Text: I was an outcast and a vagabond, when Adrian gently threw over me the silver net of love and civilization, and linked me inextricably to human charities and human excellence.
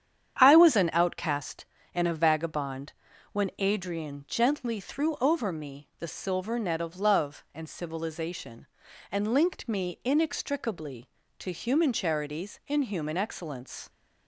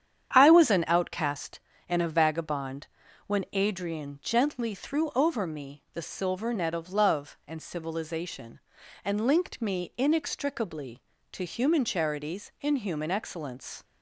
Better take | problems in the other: neither | starts louder than the rest; strong; the same in both

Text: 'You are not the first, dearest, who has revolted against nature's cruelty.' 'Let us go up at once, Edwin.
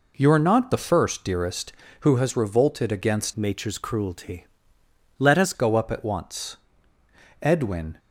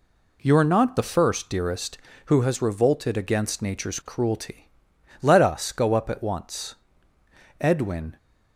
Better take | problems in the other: second | changes voice from "nature's" to "us"; from 3.3 to 5.5 s; 2.2 s long

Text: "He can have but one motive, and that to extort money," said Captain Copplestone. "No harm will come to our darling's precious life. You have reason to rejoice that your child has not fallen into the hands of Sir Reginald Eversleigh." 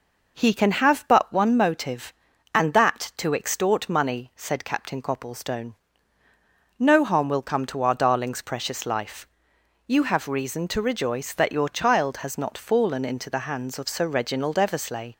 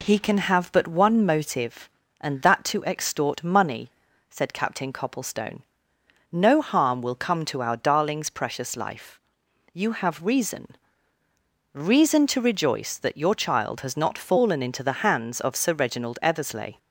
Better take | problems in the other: first | says "reason" twice; at 11.7 s

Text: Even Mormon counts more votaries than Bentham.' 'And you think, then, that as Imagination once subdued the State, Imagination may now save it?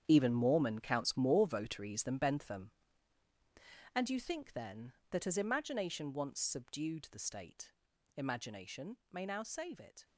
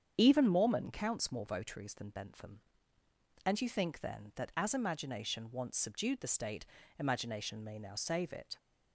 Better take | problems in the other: second | gets quieter; strong; throughout; 12 dB // starts louder than the rest; strong; until 1.0 s; 8.5 dB; strong in the second

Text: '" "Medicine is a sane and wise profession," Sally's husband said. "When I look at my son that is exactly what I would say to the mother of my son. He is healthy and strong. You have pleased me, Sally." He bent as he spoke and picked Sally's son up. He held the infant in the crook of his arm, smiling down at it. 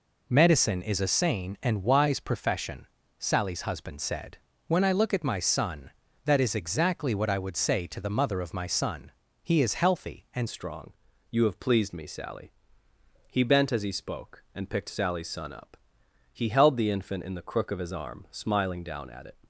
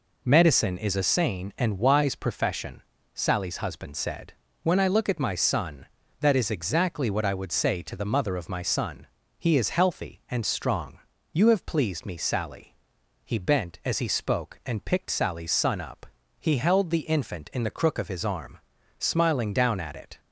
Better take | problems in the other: second | changes voice at "strong"; from 10.4 s on; 8.9 s long

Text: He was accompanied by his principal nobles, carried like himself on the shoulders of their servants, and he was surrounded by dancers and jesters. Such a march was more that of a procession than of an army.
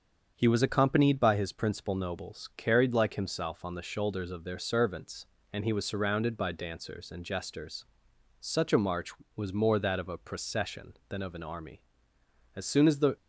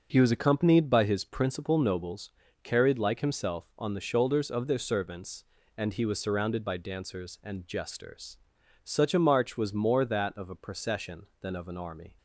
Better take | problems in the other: second | starts louder than the rest; strong; until 1.3 s; 7 dB; also in the second // goes on to say "As soon as the"; from 12.5 s on; 0.60 s long

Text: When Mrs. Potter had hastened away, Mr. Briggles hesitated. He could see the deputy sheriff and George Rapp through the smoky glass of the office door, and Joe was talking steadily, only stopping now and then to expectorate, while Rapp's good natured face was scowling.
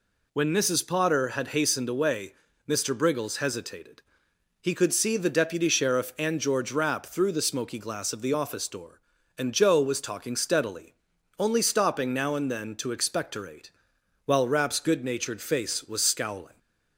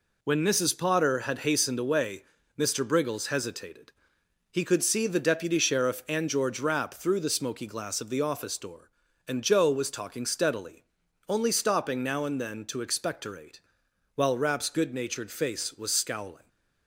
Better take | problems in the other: first | gets quieter; throughout; 6.5 dB

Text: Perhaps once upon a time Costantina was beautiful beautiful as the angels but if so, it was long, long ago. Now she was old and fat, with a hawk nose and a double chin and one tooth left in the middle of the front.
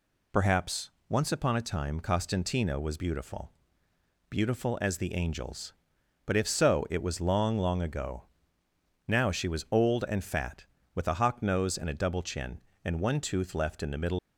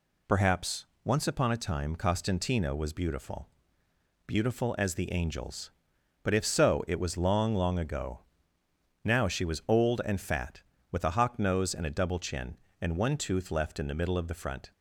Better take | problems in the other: second | pauses between "Perhaps" and "once"; slight; at 0.8 s; 0.18 s long; slight in the second // pauses between "beautiful" and "beautiful"; noticeable; at 3.5 s; 0.76 s long; noticeable in the second // stops before "of the front"; at 14.1 s

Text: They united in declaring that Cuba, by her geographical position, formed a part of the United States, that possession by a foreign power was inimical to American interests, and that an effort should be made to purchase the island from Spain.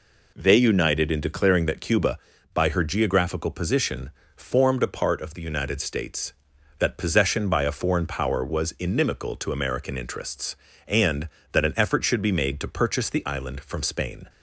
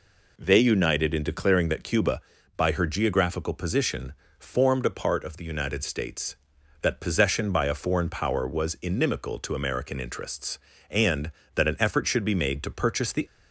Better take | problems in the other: first | stops before "island from Spain"; at 13.2 s

